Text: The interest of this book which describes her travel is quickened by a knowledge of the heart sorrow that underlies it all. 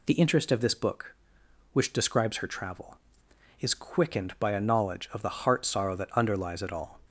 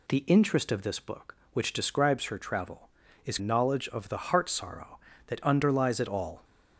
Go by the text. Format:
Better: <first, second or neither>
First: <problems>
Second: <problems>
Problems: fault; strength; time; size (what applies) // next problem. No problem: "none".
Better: first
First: none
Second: skips "quickened by a"; at 3.3 s